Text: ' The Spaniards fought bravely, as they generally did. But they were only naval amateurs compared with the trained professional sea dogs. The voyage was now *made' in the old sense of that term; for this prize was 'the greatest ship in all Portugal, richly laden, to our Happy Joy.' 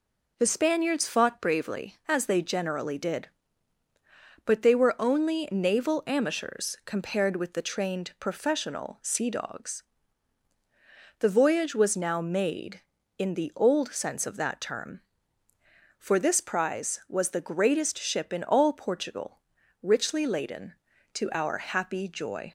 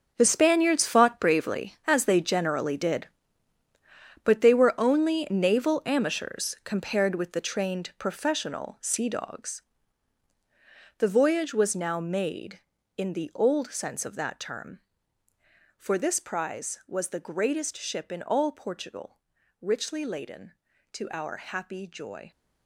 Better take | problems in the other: first | gets quieter; strong; throughout; 12.5 dB

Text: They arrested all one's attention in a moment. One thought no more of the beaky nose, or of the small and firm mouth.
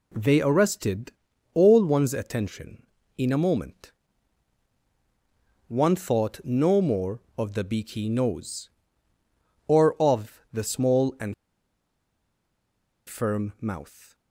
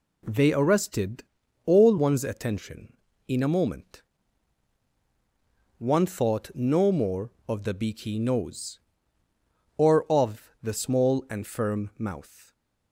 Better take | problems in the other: second | pauses between "arrested" and "all"; at 1.1 s; 0.44 s long; also in the second // pauses between "and" and "firm"; strong; at 11.3 s; 1.7 s long

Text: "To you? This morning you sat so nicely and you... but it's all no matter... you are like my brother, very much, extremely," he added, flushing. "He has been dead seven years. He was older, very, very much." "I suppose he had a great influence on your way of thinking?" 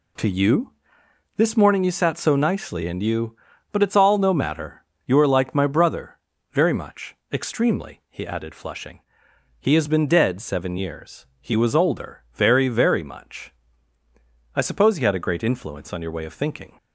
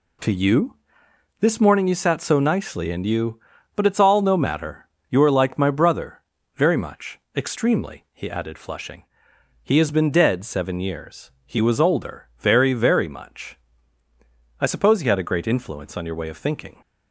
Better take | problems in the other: neither | none

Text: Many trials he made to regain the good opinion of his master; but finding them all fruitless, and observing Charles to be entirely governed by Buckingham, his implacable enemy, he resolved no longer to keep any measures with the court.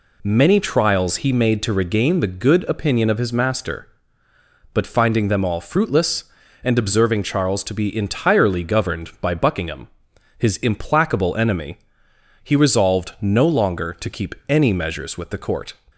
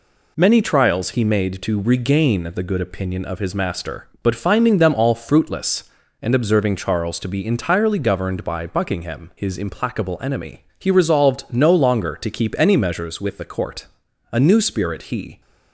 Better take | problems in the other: first | goes on to say "A new spirit he"; noticeable; from 14.3 s on; 1.0 s long

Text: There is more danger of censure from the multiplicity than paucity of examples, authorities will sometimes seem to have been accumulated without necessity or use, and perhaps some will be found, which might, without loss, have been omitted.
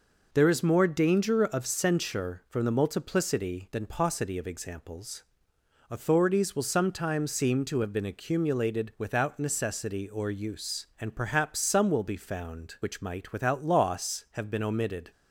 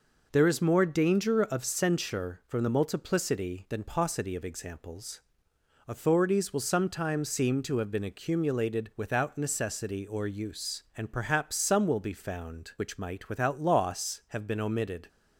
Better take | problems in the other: neither | none

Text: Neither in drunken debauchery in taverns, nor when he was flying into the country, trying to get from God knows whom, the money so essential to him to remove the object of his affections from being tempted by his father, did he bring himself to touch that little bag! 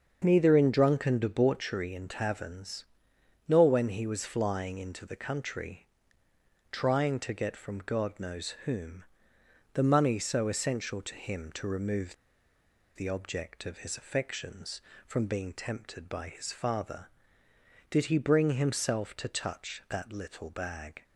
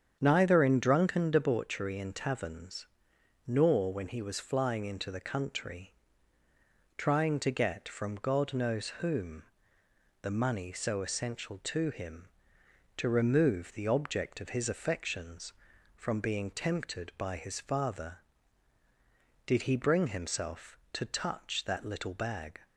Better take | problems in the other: second | starts louder than the rest; until 1.2 s; 7 dB; strong in the second // pauses between "remove" and "the"; noticeable; at 12.1 s; 0.80 s long

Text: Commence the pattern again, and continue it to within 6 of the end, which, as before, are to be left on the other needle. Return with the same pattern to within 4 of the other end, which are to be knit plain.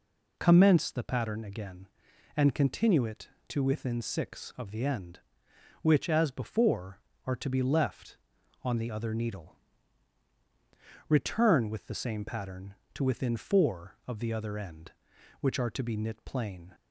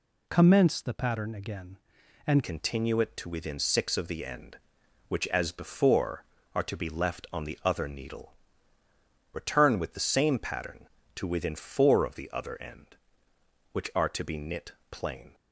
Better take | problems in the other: first | changes voice at "continue"; from 2.4 s on; 12.9 s long // pauses between "knit" and "plain"; slight; at 14.7 s; 0.18 s long

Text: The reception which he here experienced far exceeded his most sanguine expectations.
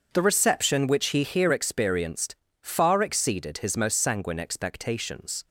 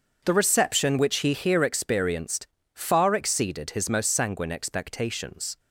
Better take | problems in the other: neither | starts louder than the rest; the same in both // pauses between "experienced" and "far"; slight; the same in both

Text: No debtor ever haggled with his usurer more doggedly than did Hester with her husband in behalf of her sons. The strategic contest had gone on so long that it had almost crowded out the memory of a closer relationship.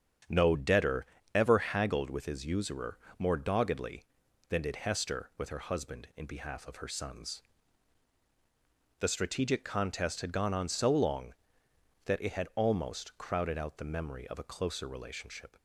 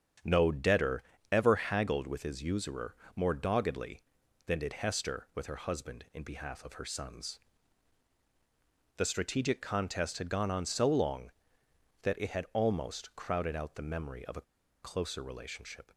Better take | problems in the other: first | starts louder than the rest; strong; until 1.5 s; 8 dB; strong in the first // pauses between "debtor" and "ever"; slight; at 1.0 s; 0.28 s long; slight in the first // pauses between "usurer" and "more"; slight; at 2.9 s; 0.20 s long; slight in the first // pauses between "a" and "closer"; at 14.4 s; 0.39 s long

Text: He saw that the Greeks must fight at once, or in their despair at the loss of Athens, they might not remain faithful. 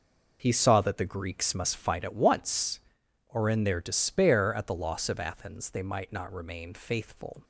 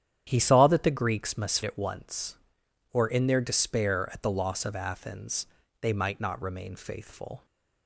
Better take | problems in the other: first | starts louder than the rest; strong; until 1.2 s; 10 dB // skips "fight"; at 1.6 s

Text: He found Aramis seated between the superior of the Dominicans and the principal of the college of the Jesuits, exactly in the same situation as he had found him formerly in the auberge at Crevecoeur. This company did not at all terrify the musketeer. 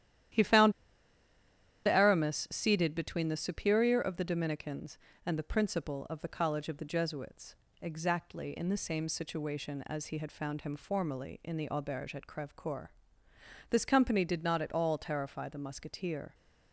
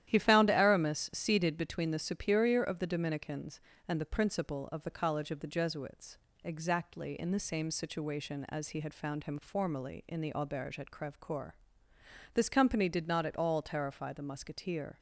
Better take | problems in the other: second | starts louder than the rest; strong; until 2.4 s; 11.5 dB; strong in the second // pauses between "found" and "Aramis"; at 0.7 s; 1.1 s long

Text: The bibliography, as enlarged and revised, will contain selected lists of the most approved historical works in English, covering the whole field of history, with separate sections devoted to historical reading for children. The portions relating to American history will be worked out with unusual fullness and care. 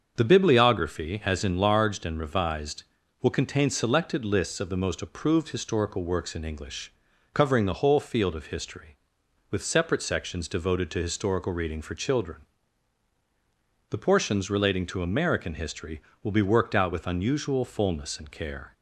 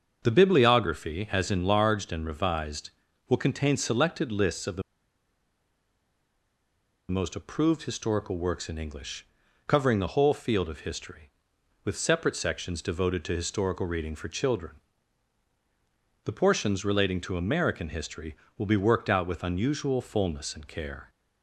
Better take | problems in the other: first | starts louder than the rest; until 1.2 s; 7 dB; also in the first // pauses between "the" and "most"; strong; at 4.8 s; 2.2 s long

